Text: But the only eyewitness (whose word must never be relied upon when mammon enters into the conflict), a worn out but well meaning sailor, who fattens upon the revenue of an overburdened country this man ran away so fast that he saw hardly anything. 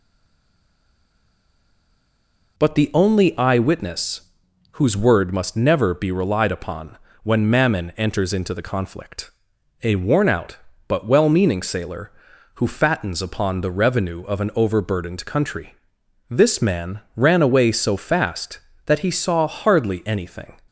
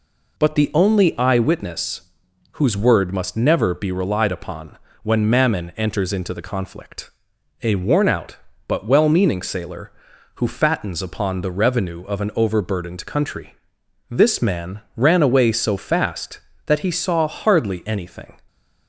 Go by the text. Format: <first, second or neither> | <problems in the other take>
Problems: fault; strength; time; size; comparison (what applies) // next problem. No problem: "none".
second | stays silent before the first word; strong; until 2.5 s; 2.5 s long // pauses between "upon" and "when"; slight; at 6.9 s; 0.26 s long; slight in the second // pauses between "country" and "this"; noticeable; at 15.7 s; 0.56 s long; noticeable in the second // pauses between "man" and "ran"; slight; at 16.9 s; 0.16 s long; slight in the second